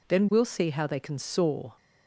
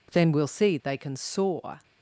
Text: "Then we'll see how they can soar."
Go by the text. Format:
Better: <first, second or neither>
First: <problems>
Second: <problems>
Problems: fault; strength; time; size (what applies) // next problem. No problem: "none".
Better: first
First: none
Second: skips "how"; at 0.8 s